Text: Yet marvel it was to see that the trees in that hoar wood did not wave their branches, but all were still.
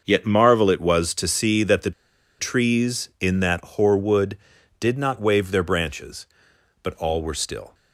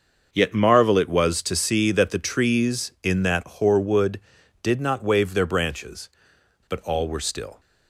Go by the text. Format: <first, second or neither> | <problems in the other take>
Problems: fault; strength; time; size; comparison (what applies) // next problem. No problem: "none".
second | starts louder than the rest; noticeable; until 1.0 s; 6 dB; also in the second // pauses between "the" and "trees"; noticeable; at 1.9 s; 0.48 s long